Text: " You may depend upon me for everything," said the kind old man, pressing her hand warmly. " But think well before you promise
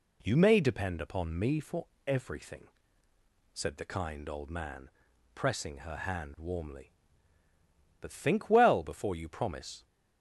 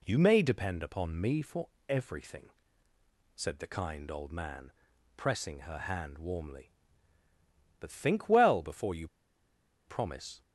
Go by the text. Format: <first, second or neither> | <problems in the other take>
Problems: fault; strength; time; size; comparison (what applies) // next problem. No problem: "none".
first | pauses between "for" and "everything"; slight; at 1.6 s; 0.18 s long; slight in the first // pauses between "you" and "promise"; noticeable; at 9.0 s; 0.79 s long